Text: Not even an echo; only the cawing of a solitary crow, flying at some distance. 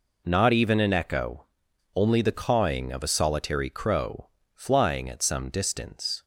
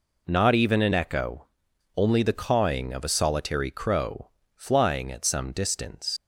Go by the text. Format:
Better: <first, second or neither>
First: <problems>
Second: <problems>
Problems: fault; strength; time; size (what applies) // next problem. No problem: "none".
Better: first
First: none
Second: leaves "distance" unfinished; at 6.1 s; 95 ms